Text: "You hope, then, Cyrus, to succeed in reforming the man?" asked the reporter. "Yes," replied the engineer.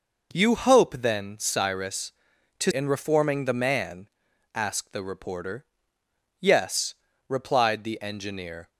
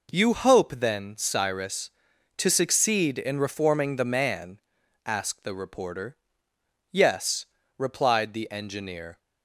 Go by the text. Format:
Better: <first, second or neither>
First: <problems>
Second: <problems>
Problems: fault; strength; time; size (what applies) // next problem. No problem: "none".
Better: second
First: skips "succeed"; at 2.7 s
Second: none